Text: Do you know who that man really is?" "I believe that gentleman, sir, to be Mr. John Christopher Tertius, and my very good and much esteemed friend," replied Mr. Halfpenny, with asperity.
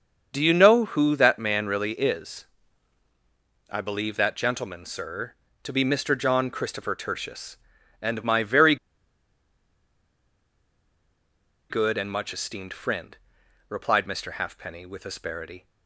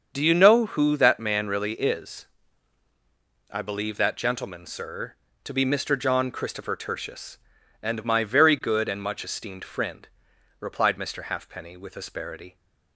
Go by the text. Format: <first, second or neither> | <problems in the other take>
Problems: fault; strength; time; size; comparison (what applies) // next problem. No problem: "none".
second | starts louder than the rest; until 1.3 s; 7 dB; also in the second // pauses between "very" and "good"; strong; at 8.7 s; 2.9 s long